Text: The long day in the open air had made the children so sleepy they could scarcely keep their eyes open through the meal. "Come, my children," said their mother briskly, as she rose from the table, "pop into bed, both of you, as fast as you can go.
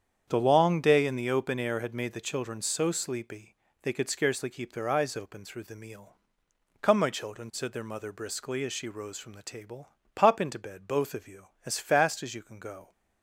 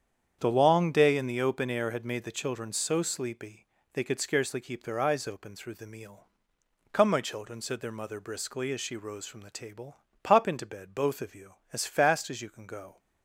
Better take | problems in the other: neither | starts louder than the rest; strong; the same in both // pauses between "sleepy" and "they"; slight; the same in both

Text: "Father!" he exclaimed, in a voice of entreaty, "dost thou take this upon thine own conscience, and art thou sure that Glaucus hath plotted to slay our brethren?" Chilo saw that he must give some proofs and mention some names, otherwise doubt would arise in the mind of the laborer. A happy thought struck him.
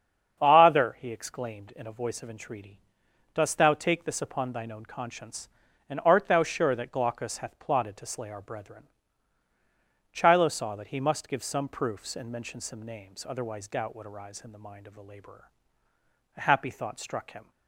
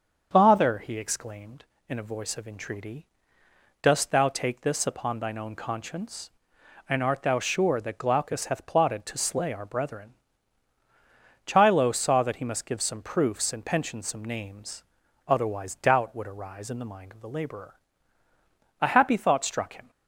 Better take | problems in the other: first | starts louder than the rest; until 1.3 s; 7 dB; strong in the first // says "pension" for "mention"; at 13.6 s

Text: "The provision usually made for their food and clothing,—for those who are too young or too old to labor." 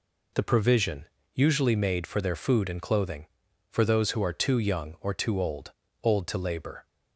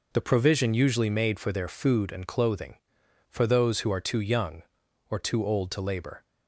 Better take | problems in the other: second | pauses between "provision" and "usually"; slight; at 1.0 s; 0.30 s long // says "old" twice; at 6.0 s

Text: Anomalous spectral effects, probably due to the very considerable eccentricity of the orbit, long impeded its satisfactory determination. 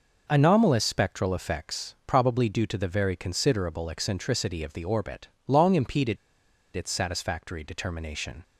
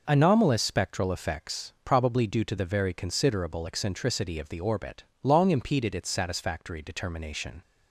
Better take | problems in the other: second | pauses between "impeded" and "its"; noticeable; at 6.1 s; 0.59 s long

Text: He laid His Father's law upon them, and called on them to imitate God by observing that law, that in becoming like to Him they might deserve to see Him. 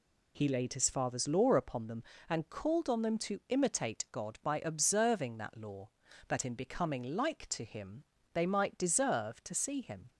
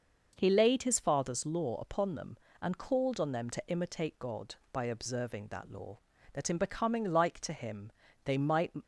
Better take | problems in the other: first | pauses between "Him" and "they"; slight; at 7.9 s; 0.32 s long; slight in the first // stops before "deserve to see Him"; at 8.8 s

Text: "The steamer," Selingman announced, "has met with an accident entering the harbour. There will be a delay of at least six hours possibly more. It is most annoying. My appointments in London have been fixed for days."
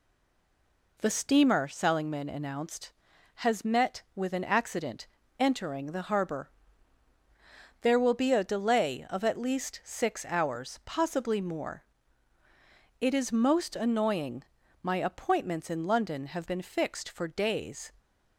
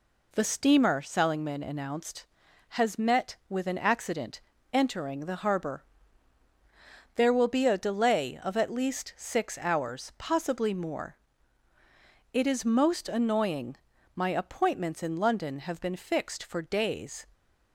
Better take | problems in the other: second | stays silent before the first word; until 0.9 s; 0.9 s long // pauses between "accident" and "entering"; slight; at 5.0 s; 0.34 s long; slight in the second

